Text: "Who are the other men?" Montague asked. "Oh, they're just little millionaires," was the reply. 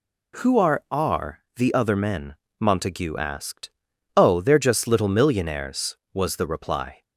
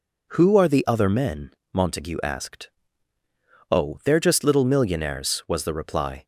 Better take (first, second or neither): second